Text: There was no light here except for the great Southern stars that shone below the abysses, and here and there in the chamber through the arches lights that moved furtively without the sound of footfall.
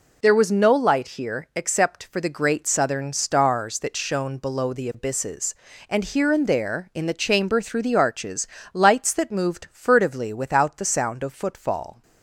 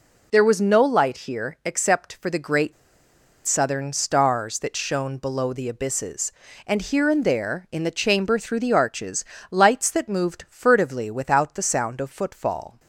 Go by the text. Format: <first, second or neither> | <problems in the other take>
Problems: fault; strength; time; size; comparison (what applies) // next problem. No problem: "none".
first | pauses between "great" and "Southern"; noticeable; at 2.7 s; 0.71 s long // pauses between "arches" and "lights"; slight; at 9.2 s; 0.28 s long; slight in the first